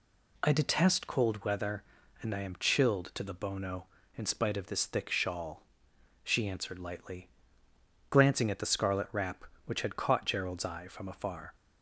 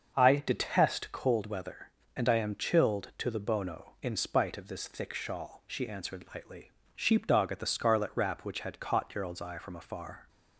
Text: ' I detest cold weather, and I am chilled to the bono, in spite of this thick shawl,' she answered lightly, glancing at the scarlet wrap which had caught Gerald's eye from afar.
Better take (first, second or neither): first